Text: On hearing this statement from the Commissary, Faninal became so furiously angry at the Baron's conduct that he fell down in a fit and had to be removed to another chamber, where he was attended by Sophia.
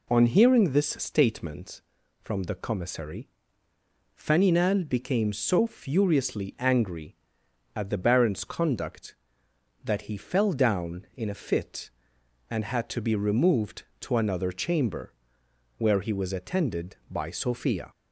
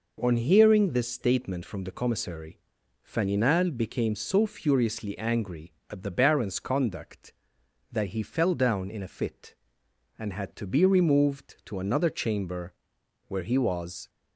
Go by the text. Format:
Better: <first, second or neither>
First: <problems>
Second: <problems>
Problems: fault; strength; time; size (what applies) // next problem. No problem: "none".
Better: first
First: none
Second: stops before "attended by Sophia"; at 14.0 s